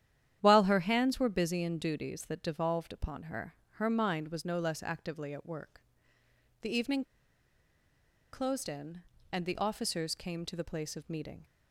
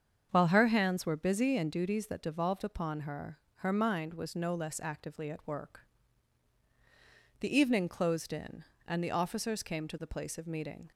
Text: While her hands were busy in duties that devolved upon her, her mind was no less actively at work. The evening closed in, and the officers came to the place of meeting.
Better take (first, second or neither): second